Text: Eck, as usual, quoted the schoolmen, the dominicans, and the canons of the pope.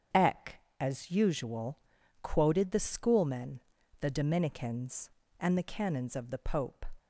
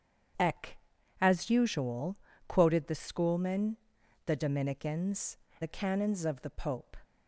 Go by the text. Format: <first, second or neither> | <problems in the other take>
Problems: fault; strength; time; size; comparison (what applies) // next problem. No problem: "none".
first | starts louder than the rest; strong; until 1.8 s; 8 dB; strong in the first // skips "and"; at 5.4 s